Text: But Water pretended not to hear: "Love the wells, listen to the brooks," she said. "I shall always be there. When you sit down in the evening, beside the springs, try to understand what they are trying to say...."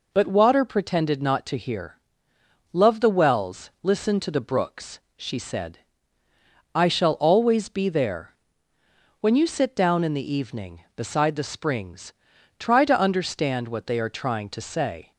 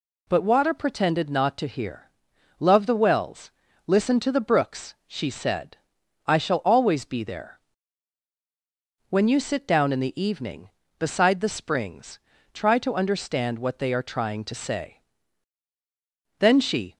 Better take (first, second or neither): first